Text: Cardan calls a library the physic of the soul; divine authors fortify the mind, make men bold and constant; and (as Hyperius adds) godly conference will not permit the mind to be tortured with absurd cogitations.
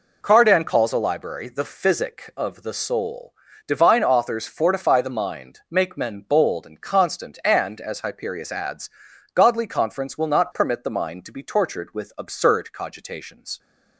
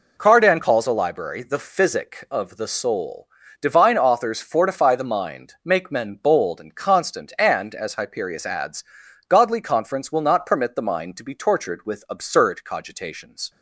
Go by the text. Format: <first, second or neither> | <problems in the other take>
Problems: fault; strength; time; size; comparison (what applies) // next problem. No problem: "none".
neither | none